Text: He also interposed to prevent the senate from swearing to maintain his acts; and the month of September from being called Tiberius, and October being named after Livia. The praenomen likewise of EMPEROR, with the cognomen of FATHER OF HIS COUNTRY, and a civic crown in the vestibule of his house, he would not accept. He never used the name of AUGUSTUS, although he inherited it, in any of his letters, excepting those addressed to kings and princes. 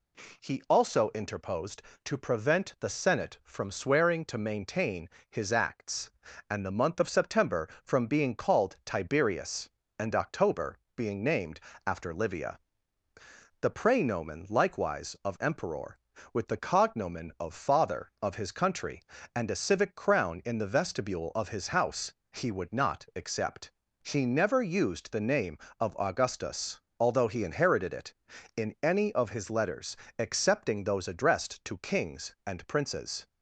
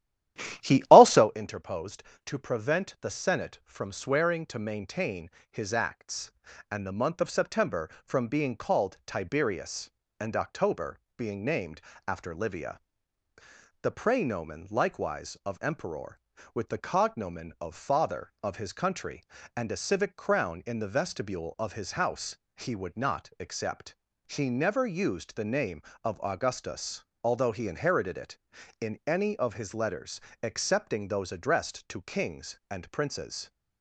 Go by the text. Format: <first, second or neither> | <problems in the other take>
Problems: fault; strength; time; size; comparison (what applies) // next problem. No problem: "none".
first | starts louder than the rest; strong; until 1.3 s; 12.5 dB // pauses between "maintain" and "his"; slight; at 5.3 s; 0.18 s long; slight in the first // pauses between "October" and "being"; slight; at 10.9 s; 0.16 s long; slight in the first // pauses between "named" and "after"; slight; at 11.8 s; 0.24 s long; slight in the first